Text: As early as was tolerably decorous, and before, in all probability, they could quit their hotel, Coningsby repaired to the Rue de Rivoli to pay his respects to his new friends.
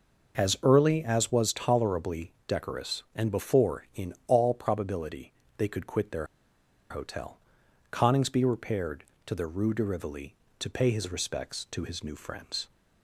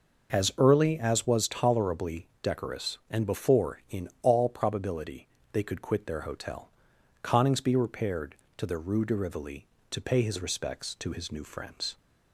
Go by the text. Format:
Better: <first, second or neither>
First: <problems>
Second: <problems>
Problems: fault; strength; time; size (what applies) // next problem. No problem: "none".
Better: second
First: pauses between "tolerably" and "decorous"; slight; at 2.2 s; 0.16 s long // pauses between "their" and "hotel"; noticeable; at 6.2 s; 0.64 s long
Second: pauses between "tolerably" and "decorous"; slight; at 2.2 s; 0.16 s long